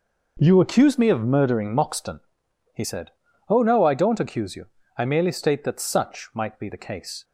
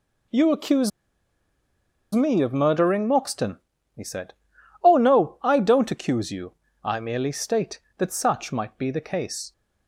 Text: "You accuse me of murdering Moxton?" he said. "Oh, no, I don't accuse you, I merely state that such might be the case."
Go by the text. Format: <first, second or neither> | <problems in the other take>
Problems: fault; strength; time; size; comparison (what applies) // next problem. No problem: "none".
first | pauses between "accuse" and "me"; at 0.9 s; 1.2 s long